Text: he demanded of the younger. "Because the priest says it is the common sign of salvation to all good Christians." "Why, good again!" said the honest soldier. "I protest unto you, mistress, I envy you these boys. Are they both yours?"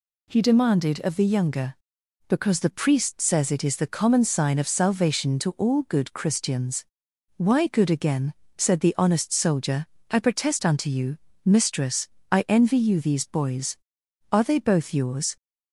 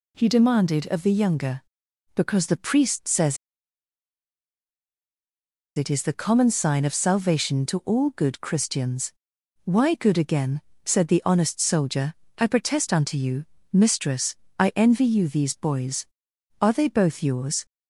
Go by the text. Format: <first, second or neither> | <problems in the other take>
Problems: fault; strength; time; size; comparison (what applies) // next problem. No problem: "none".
first | pauses between "says" and "it"; strong; at 3.3 s; 2.4 s long